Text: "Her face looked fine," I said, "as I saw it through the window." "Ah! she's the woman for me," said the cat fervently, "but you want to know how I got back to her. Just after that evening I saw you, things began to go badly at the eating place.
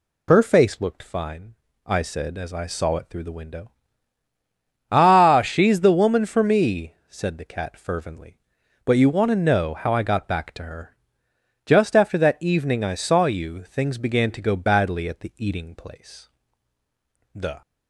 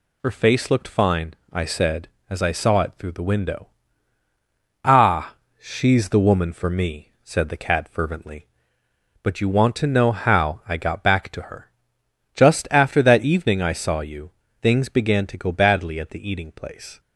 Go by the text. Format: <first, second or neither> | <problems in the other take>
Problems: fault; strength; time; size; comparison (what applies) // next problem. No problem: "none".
second | goes on to say "The"; slight; from 17.3 s on; 0.28 s long